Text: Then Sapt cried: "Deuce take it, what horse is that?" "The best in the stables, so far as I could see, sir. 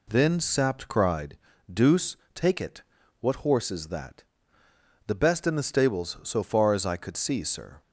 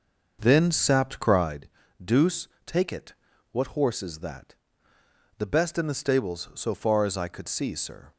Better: first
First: pauses between "Deuce" and "take"; slight; at 2.1 s; 0.16 s long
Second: starts louder than the rest; noticeable; until 1.6 s; 6 dB // pauses between "Deuce" and "take"; slight; at 2.4 s; 0.16 s long

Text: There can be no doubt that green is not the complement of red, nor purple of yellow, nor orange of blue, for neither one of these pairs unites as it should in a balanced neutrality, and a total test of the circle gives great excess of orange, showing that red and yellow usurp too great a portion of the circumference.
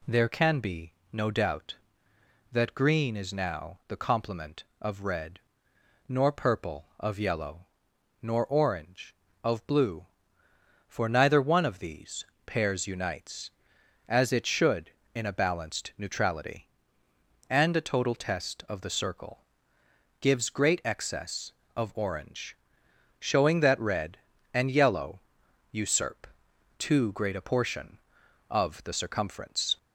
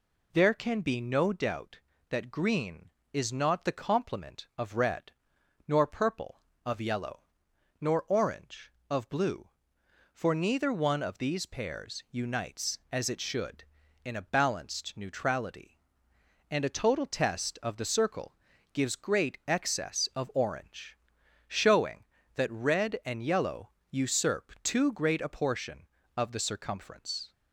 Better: second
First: pauses between "be" and "no"; slight; at 0.9 s; 0.20 s long // says "now" for "not"; at 3.3 s // pauses between "these" and "pairs"; slight; at 12.2 s; 0.20 s long // pauses between "circle" and "gives"; noticeable; at 19.4 s; 0.74 s long // pauses between "yellow" and "usurp"; noticeable; at 25.2 s; 0.50 s long // pauses between "usurp" and "too"; noticeable; at 26.2 s; 0.50 s long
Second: pauses between "circle" and "gives"; slight; at 18.3 s; 0.36 s long // pauses between "yellow" and "usurp"; slight; at 23.7 s; 0.20 s long

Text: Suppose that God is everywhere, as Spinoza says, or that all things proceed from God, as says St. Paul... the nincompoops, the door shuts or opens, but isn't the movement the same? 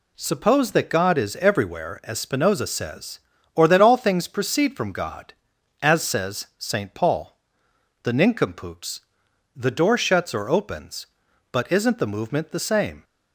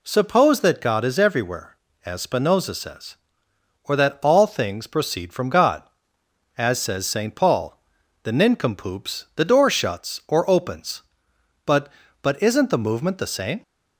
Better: first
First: none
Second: says "but" twice; at 12.2 s

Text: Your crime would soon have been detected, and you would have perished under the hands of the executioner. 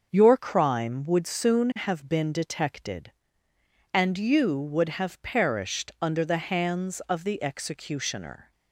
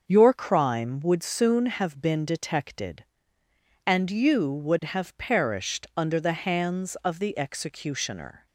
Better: neither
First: starts louder than the rest; until 1.1 s; 6.5 dB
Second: starts louder than the rest; until 1.0 s; 6.5 dB

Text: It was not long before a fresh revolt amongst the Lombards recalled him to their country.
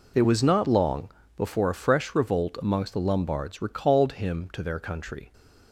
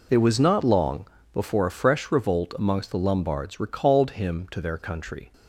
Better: neither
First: pauses between "long" and "before"; slight; at 1.1 s; 0.26 s long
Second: pauses between "long" and "before"; slight; at 1.0 s; 0.26 s long

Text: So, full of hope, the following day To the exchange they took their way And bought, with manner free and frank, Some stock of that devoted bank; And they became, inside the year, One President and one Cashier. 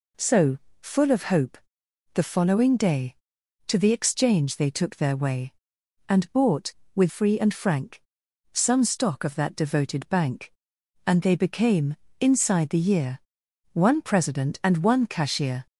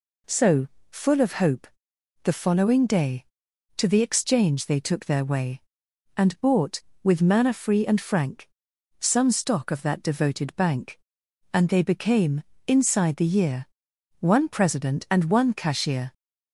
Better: second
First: skips "manner"; at 7.0 s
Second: none

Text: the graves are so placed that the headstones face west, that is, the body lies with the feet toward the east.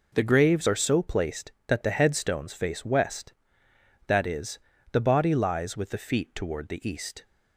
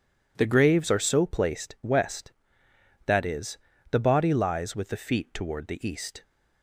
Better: first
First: none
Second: skips "that the headstones face"; at 1.7 s

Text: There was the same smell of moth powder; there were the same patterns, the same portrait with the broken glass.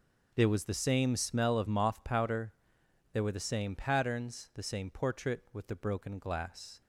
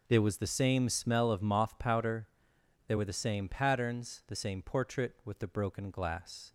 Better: neither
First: none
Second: none

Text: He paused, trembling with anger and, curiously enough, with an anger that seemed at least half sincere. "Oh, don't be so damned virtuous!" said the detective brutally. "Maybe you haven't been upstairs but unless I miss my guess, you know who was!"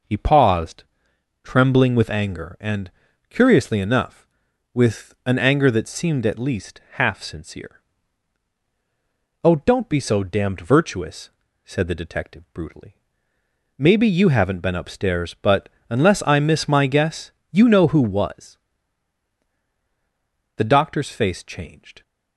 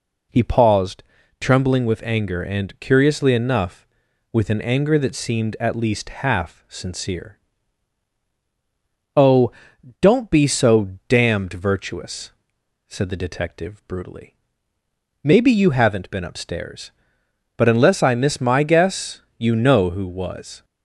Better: second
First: pauses between "but" and "unless"; slight; at 15.6 s; 0.20 s long // goes on to say "The Doctor's face changed"; from 20.5 s on; 1.4 s long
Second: none

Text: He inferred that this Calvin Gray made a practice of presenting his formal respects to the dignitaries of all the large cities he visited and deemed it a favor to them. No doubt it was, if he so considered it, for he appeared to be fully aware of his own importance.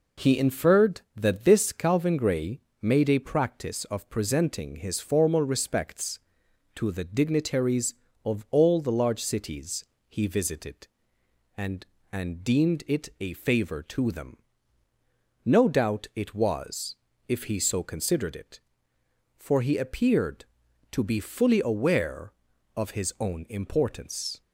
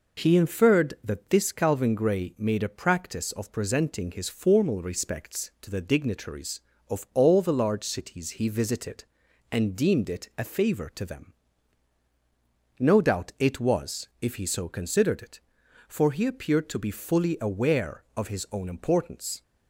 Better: second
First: pauses between "Gray" and "made"; slight; at 2.5 s; 0.22 s long // pauses between "cities" and "he"; slight; at 9.8 s; 0.24 s long // says "and" twice; at 12.1 s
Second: none

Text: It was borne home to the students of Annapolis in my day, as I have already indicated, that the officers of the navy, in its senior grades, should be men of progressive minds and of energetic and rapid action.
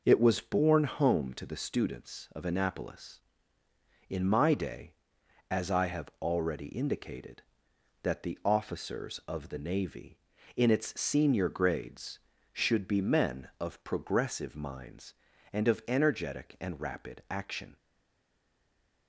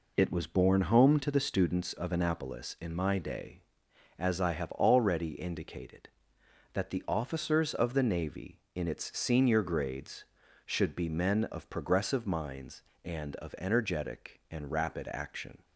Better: second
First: stays silent after the last word; noticeable; from 17.7 s on; 1.3 s long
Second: none

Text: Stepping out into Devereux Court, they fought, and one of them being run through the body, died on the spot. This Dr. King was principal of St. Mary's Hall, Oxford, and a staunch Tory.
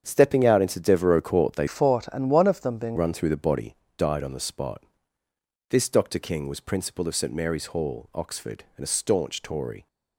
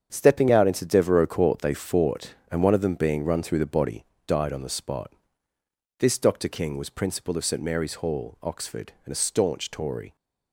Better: second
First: starts louder than the rest; strong; until 1.0 s; 8 dB // changes voice from "fought" to "being"; from 1.6 to 2.9 s; 1.3 s long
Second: starts louder than the rest; strong; until 1.1 s; 7.5 dB

